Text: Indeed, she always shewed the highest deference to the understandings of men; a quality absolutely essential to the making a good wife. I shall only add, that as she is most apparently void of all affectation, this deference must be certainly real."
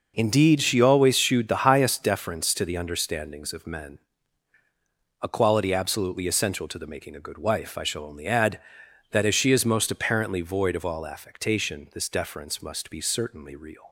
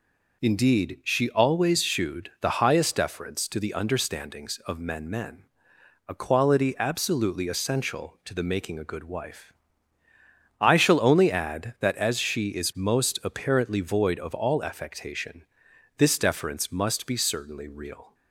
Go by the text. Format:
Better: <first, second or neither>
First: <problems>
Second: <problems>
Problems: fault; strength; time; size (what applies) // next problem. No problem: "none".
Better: first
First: none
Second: says "men" twice; at 5.0 s